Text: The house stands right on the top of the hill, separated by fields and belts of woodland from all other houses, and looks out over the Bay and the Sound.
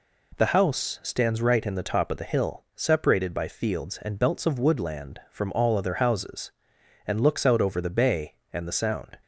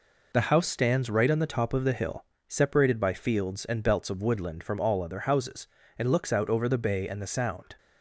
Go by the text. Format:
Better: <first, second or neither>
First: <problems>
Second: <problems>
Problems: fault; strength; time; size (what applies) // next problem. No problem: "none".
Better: second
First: says "in" for "on"; at 1.6 s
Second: none